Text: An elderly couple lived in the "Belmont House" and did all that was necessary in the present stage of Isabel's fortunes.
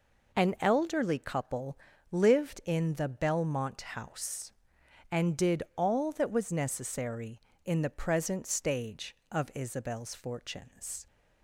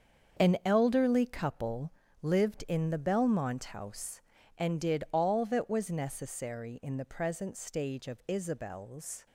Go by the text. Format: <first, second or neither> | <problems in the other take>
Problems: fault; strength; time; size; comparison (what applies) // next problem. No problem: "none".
first | starts louder than the rest; until 1.4 s; 7 dB // pauses between "couple" and "lived"; slight; at 1.9 s; 0.30 s long; slight in the first // stops before "fortunes"; at 9.2 s